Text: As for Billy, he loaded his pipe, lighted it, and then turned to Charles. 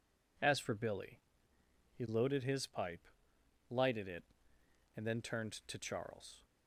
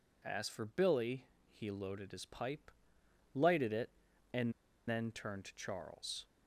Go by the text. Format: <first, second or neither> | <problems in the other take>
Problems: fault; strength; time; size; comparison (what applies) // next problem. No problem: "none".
first | pauses between "and" and "then"; at 4.5 s; 0.37 s long